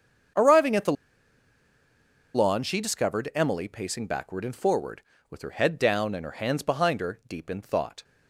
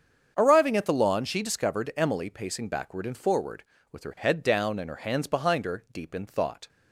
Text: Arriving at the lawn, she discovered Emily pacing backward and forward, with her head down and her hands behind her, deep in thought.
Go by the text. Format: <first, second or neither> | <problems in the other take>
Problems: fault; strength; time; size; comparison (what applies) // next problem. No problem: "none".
second | starts louder than the rest; strong; until 2.7 s; 7 dB; strong in the second // pauses between "the" and "lawn"; strong; at 0.9 s; 1.4 s long